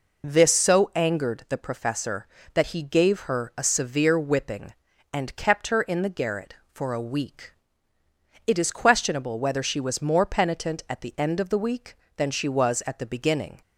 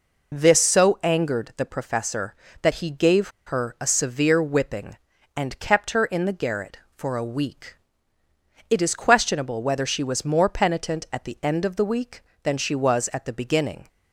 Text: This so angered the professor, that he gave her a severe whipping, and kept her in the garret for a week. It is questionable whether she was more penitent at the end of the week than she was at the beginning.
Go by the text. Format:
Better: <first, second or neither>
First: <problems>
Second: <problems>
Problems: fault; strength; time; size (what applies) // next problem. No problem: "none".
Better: first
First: none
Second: pauses between "gave" and "her"; slight; at 3.2 s; 0.17 s long